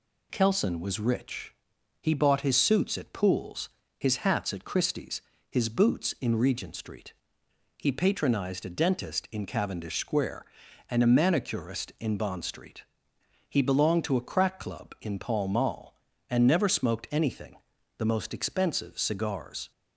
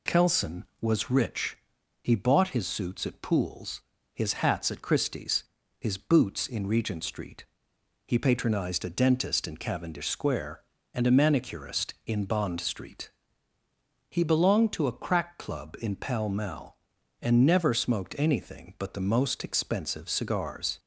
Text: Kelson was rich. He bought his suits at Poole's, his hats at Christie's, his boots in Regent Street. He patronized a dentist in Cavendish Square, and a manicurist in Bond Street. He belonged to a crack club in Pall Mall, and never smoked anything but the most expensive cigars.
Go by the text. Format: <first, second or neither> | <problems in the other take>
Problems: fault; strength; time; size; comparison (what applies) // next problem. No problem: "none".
second | skips "but"; at 17.7 s